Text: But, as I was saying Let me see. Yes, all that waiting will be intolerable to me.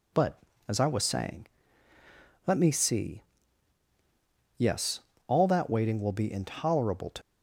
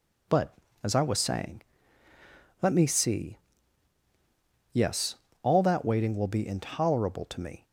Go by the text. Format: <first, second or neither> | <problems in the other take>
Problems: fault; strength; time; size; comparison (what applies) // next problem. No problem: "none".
second | pauses between "saying" and "Let"; at 1.4 s; 1.0 s long; also in the second // stops before "me"; at 7.2 s